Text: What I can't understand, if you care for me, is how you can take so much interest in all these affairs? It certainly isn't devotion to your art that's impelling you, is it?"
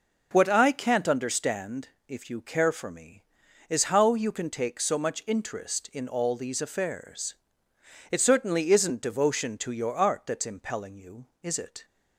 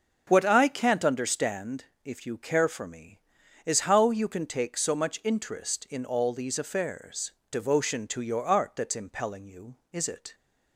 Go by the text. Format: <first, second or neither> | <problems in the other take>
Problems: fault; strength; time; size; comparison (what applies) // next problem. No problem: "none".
first | starts louder than the rest; noticeable; until 1.2 s; 6 dB // skips "It certainly isn't"; at 7.4 s